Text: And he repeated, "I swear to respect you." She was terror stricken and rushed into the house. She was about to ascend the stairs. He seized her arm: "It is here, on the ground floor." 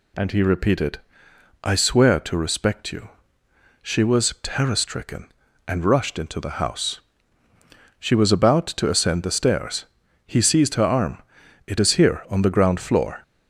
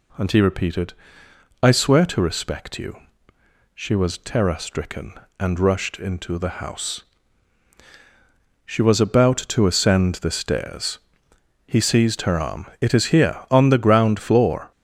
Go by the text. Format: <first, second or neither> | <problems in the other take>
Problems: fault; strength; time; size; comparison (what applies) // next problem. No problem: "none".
neither | none